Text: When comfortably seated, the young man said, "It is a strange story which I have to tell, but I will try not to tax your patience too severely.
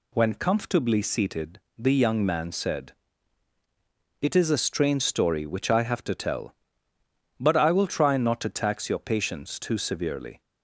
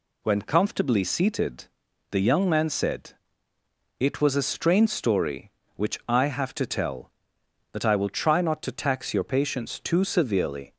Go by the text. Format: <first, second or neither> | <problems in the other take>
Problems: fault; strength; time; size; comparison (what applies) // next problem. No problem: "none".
first | says "was" for "is"; at 4.2 s